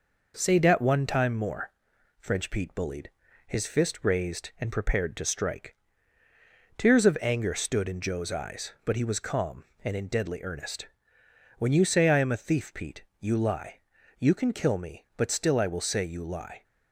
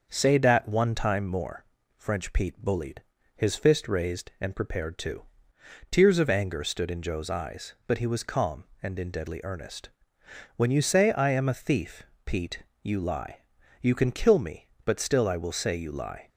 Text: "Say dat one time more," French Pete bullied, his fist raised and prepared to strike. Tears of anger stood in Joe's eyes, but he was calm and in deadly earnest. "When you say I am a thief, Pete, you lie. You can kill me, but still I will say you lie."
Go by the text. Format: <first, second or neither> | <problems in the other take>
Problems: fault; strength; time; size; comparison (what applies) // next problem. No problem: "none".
first | starts louder than the rest; until 1.1 s; 6.5 dB // skips "strike"; at 5.5 s